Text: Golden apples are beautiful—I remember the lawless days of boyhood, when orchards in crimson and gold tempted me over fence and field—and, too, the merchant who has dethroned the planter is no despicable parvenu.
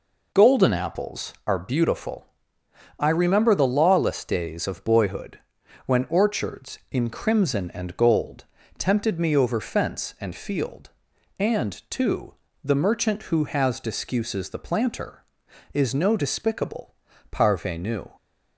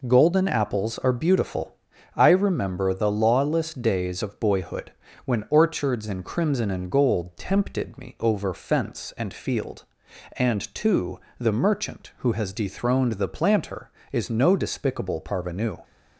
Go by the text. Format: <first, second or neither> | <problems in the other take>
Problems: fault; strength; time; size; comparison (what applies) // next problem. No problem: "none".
second | pauses between "gold" and "tempted"; slight; at 8.4 s; 0.32 s long // says "discuses" for "dethroned"; at 13.7 s // pauses between "despicable" and "parvenu"; at 16.9 s; 0.38 s long